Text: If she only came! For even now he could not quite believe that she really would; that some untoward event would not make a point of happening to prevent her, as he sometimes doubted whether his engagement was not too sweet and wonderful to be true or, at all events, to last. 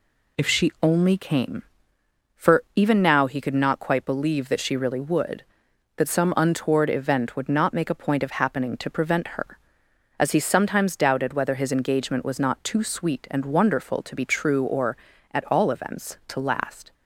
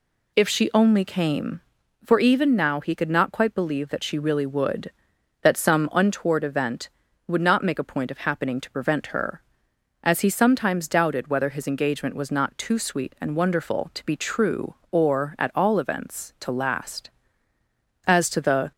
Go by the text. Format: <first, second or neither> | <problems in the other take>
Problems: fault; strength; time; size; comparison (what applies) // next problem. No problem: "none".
first | goes on to say "As to the"; noticeable; from 18.0 s on; 0.64 s long